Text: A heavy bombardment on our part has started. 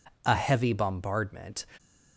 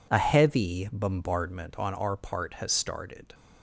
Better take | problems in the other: second | stops before "on our part has started"; at 1.7 s

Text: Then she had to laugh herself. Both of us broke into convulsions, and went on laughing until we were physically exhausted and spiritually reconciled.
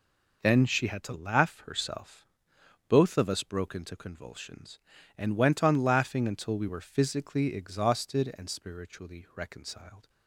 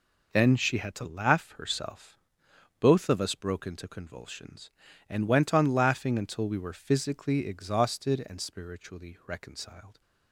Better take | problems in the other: neither | none

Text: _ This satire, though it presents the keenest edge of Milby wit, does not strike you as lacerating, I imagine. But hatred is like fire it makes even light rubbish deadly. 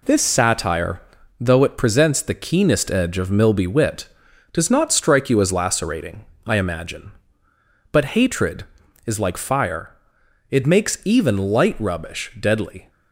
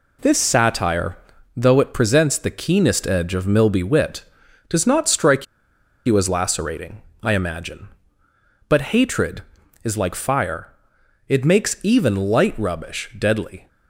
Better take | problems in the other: first | pauses between "strike" and "you"; noticeable; at 5.4 s; 0.60 s long // pauses between "fire" and "it"; noticeable; at 10.6 s; 0.60 s long; noticeable in the first

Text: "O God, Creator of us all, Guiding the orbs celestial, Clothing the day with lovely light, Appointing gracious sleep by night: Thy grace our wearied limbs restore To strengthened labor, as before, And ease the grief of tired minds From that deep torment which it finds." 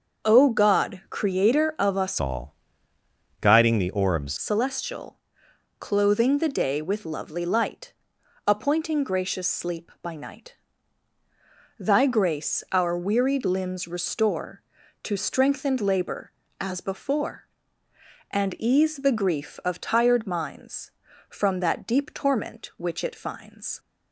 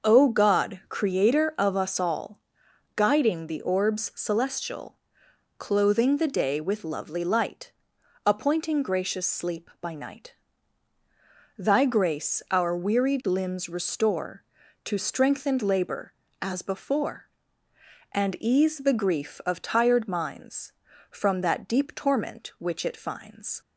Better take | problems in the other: second | starts louder than the rest; until 1.3 s; 6.5 dB; noticeable in the second // changes voice from "all" to "orbs"; from 2.2 to 4.3 s; 2.1 s long

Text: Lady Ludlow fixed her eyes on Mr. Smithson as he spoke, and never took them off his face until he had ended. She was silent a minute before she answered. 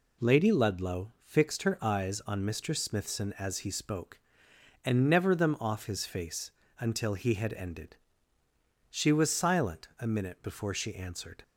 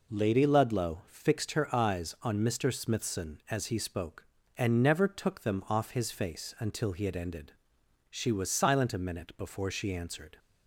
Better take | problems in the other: second | skips "took"; at 5.3 s // pauses between "face" and "until"; slight; at 6.5 s; 0.28 s long

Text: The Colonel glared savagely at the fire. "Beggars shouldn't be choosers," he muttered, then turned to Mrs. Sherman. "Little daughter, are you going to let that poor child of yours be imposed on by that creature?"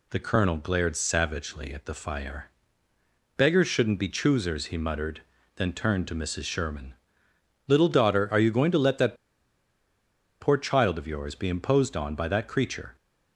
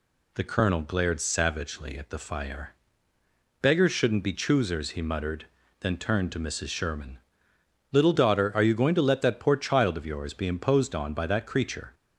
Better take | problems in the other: second | pauses between "that" and "poor"; strong; at 9.1 s; 1.2 s long

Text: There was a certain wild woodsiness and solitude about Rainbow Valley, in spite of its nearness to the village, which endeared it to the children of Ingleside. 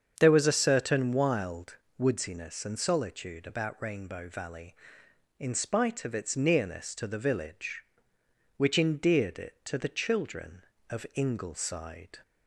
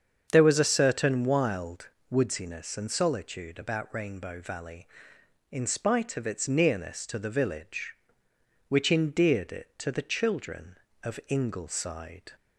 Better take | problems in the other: neither | starts louder than the rest; strong; the same in both // pauses between "wild" and "woodsiness"; slight; the same in both

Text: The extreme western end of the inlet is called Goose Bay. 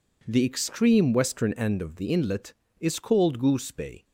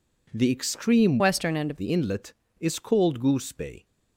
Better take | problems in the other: first | changes voice from "western" to "of"; from 1.1 to 1.7 s; 0.6 s long

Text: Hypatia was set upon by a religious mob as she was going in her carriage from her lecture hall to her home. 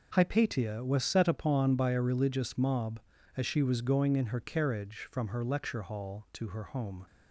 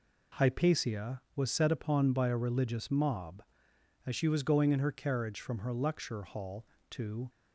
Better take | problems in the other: first | stops before "her home"; at 7.2 s

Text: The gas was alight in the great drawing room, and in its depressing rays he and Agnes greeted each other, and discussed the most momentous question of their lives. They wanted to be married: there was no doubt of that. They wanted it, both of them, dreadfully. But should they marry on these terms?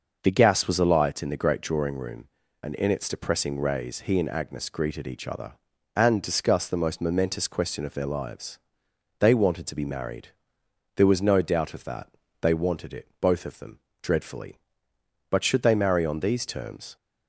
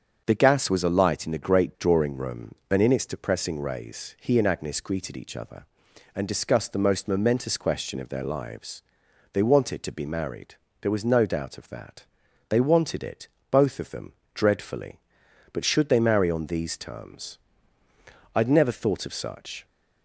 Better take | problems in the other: first | starts louder than the rest; strong; until 1.2 s; 7 dB // goes on to say "I'd never thought of such"; noticeable; from 18.3 s on; 1.3 s long

